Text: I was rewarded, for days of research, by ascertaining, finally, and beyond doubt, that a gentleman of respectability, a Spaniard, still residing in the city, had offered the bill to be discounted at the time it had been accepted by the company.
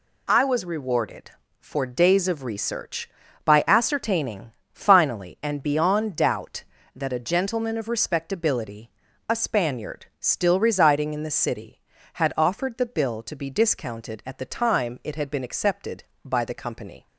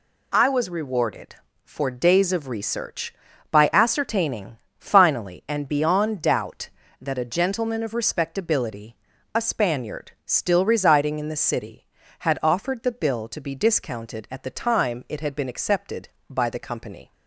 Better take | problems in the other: neither | none

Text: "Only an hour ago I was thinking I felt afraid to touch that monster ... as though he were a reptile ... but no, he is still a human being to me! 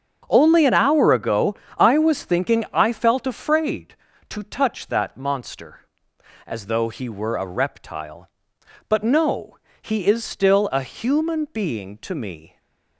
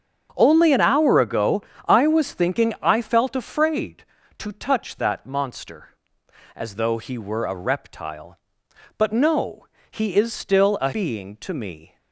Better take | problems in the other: first | starts louder than the rest; strong; until 1.3 s; 7.5 dB; strong in the first // pauses between "ago" and "I"; slight; at 1.6 s; 0.28 s long; slight in the first // skips "human"; at 10.9 s

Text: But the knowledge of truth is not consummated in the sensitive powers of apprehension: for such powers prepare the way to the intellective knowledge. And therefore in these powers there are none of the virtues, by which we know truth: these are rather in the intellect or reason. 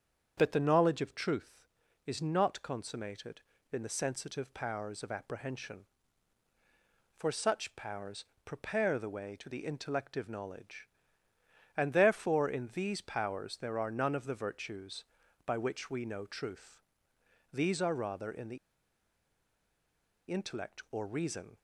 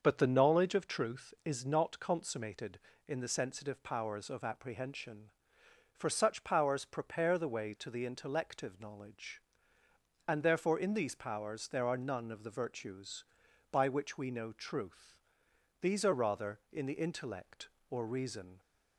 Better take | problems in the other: second | starts louder than the rest; strong; until 1.3 s; 7.5 dB; also in the second // pauses between "powers" and "prepare"; slight; at 8.2 s; 0.20 s long // pauses between "the" and "intellect"; strong; at 18.5 s; 1.7 s long

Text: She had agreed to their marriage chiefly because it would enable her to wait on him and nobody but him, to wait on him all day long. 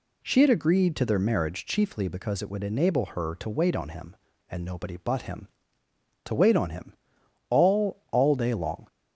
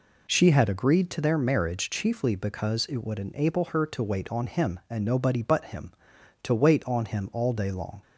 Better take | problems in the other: second | pauses between "him" and "all"; noticeable; at 6.9 s; 0.56 s long // says "all" twice; at 8.1 s

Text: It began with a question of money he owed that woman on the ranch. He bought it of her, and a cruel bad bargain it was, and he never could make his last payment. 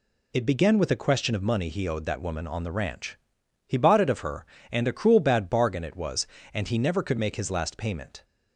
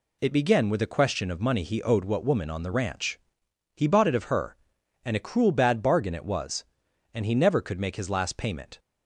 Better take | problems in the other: first | says "what" for "that"; at 2.0 s

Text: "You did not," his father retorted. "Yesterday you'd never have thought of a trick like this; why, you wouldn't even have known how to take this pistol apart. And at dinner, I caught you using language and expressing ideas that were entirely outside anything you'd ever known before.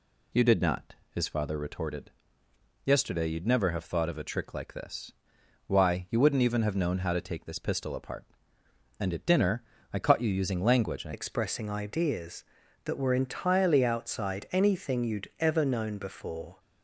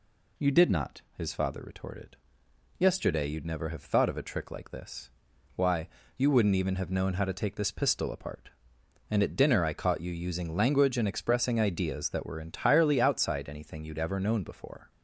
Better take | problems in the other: second | changes voice at "expressing"; from 11.1 s on; 5.4 s long

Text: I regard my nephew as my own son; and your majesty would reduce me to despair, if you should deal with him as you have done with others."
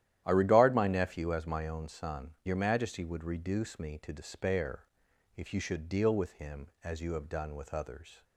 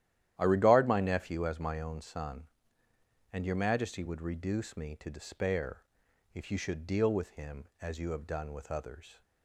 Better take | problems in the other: second | starts louder than the rest; strong; until 1.2 s; 12 dB; strong in the second // skips "and"; at 2.4 s

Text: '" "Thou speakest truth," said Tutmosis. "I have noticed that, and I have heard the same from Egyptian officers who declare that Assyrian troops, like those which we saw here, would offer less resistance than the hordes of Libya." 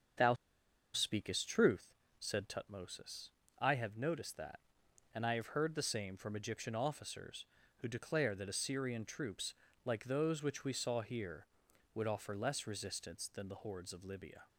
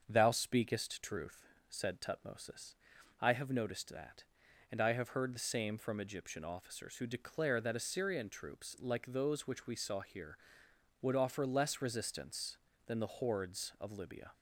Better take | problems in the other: second | starts louder than the rest; strong; until 1.7 s; 7 dB; also in the second // pauses between "Thou" and "speakest"; noticeable; at 0.3 s; 0.59 s long

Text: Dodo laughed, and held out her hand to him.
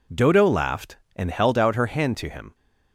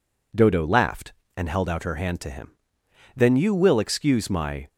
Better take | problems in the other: first | goes on to say "Then you will excuse my"; from 3.1 s on; 1.5 s long

